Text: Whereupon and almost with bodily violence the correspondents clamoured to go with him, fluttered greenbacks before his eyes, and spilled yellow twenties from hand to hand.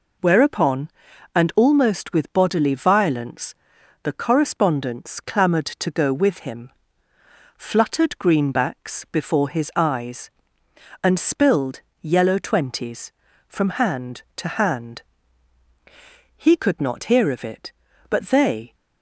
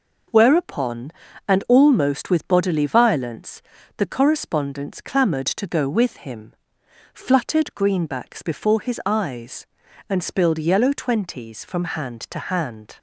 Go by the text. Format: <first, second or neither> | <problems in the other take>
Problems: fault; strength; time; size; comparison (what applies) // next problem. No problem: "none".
second | pauses between "violence" and "the"; noticeable; at 3.5 s; 0.48 s long; slight in the second // pauses between "spilled" and "yellow"; slight; at 11.8 s; 0.20 s long // goes on to say "He could not hear of it but they"; strong; from 16.3 s on; 2.3 s long